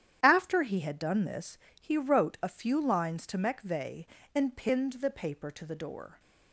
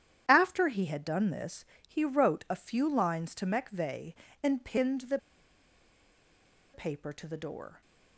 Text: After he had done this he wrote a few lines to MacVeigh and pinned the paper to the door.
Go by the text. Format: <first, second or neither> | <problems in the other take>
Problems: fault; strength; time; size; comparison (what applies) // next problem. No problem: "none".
first | starts louder than the rest; strong; until 1.3 s; 9.5 dB; strong in the first // pauses between "this" and "he"; slight; at 1.6 s; 0.20 s long; slight in the first // pauses between "the" and "paper"; strong; at 5.1 s; 1.5 s long